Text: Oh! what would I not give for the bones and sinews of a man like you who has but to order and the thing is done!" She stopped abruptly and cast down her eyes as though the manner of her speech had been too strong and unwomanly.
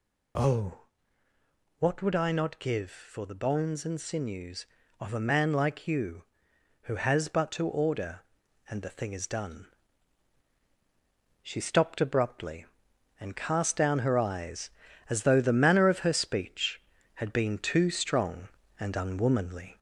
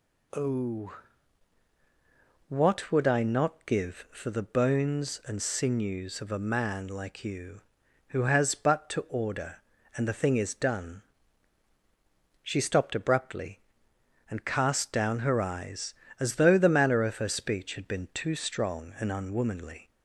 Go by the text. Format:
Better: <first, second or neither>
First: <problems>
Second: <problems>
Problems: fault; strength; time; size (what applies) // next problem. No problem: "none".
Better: second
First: gets louder; slight; throughout; 2.5 dB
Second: none